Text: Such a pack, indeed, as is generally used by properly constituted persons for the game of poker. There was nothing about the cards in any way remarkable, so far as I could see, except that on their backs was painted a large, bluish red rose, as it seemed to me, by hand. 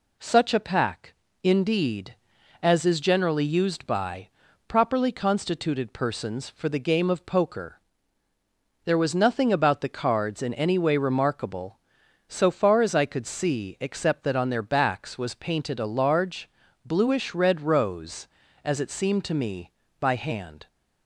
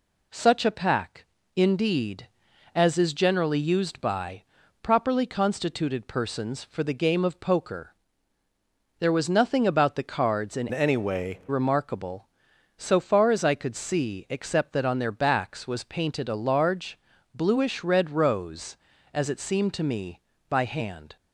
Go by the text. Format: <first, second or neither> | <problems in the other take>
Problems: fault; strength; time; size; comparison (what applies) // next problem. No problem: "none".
first | pauses between "by" and "properly"; at 4.4 s; 0.38 s long; also in the first // changes voice from "any" to "way"; from 10.7 to 11.4 s; 0.7 s long